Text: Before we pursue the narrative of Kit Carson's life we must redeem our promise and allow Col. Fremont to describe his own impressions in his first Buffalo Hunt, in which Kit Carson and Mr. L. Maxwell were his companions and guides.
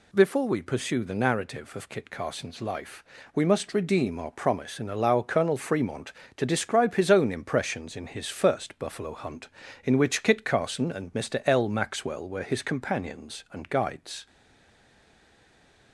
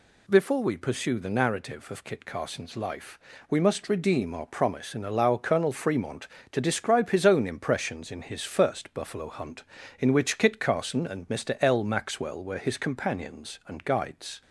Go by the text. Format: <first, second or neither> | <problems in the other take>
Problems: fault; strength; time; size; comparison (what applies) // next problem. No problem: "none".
second | pauses between "life" and "we"; slight; at 3.0 s; 0.32 s long; slight in the second // stays silent after the last word; noticeable; from 14.2 s on; 1.7 s long